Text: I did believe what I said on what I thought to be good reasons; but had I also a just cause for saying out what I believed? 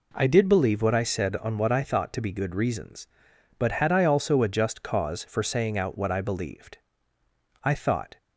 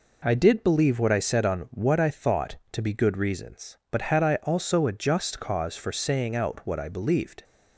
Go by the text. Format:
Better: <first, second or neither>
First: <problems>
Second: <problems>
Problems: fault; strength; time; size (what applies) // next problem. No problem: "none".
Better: second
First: goes on to say "I thought"; from 7.6 s on; 0.54 s long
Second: none